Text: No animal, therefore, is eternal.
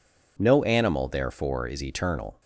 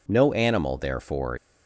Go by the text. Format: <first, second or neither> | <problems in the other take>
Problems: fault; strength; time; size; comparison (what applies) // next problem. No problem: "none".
first | stops before "is eternal"; at 1.3 s